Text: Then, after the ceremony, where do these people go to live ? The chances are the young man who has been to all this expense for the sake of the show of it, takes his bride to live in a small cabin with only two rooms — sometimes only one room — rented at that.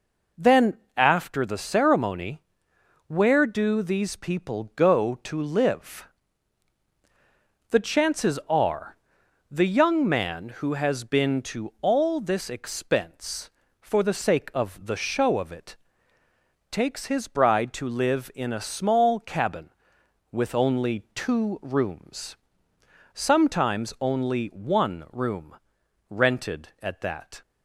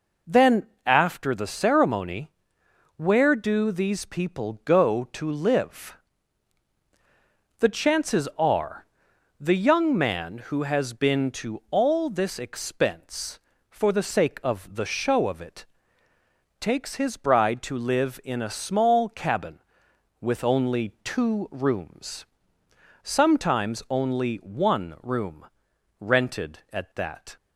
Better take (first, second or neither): neither